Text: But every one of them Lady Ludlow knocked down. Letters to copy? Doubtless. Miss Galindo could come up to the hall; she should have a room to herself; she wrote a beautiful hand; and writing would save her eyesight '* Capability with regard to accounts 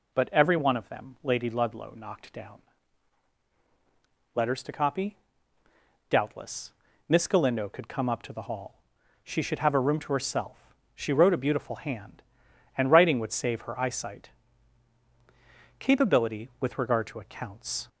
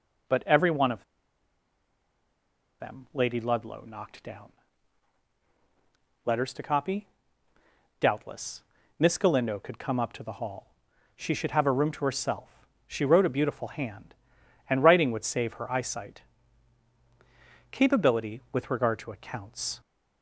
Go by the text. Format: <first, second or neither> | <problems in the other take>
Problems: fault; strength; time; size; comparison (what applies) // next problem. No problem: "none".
first | pauses between "of" and "them"; strong; at 1.0 s; 1.7 s long